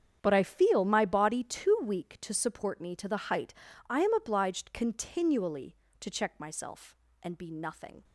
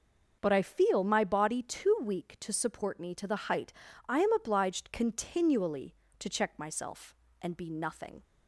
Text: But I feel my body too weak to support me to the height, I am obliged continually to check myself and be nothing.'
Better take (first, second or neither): second